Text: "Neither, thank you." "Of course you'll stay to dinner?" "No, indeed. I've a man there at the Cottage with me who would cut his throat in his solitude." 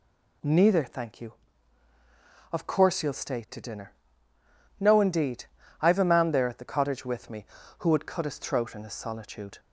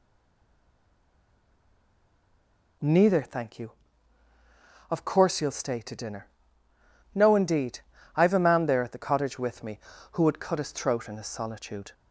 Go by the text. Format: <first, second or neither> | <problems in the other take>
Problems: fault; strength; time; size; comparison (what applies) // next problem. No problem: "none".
first | stays silent before the first word; strong; until 2.8 s; 2.8 s long